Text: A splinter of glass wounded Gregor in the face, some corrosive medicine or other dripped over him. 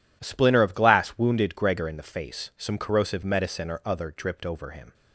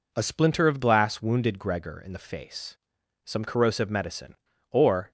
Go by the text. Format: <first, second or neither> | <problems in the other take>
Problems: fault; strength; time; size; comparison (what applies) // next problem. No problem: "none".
first | stops before "other dripped over him"; at 5.0 s